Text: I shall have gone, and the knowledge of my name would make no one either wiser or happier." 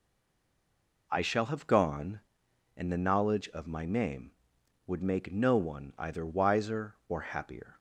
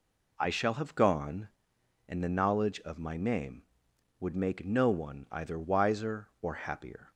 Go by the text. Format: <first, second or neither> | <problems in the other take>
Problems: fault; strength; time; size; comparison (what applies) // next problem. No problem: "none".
second | stays silent before the first word; until 1.0 s; 1.0 s long